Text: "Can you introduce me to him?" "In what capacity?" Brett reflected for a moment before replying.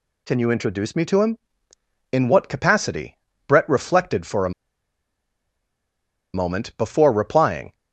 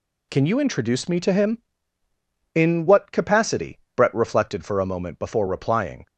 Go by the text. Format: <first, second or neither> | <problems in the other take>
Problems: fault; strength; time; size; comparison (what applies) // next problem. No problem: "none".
second | pauses between "a" and "moment"; strong; at 4.5 s; 1.8 s long